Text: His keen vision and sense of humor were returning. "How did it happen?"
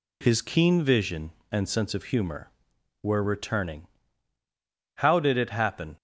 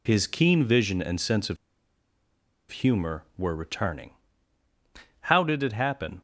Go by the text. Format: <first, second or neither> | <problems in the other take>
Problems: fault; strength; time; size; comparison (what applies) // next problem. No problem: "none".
first | pauses between "of" and "humor"; at 1.5 s; 1.1 s long